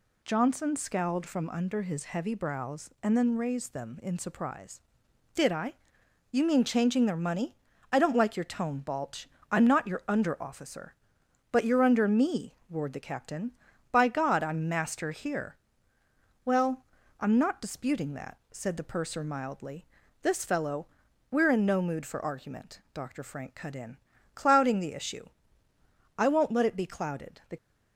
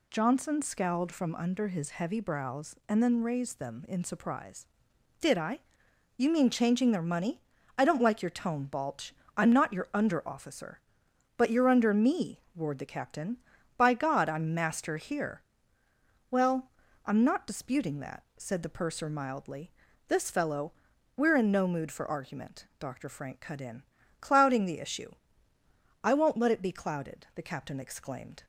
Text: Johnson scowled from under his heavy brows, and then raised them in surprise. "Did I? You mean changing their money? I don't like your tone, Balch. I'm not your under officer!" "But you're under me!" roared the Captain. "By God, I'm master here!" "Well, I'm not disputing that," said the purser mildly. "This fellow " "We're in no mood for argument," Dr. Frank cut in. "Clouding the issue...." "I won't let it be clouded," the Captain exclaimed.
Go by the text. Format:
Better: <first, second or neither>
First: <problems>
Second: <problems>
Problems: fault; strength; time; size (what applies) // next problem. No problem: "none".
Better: second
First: stops before "Captain exclaimed"; at 27.5 s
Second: none